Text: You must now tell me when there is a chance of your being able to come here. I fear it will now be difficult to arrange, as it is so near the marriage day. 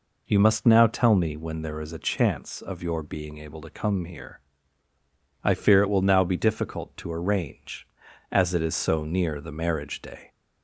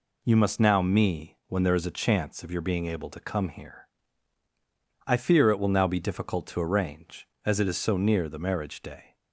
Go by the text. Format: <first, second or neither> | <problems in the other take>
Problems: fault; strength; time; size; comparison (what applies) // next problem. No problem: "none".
first | skips "tell"; at 0.8 s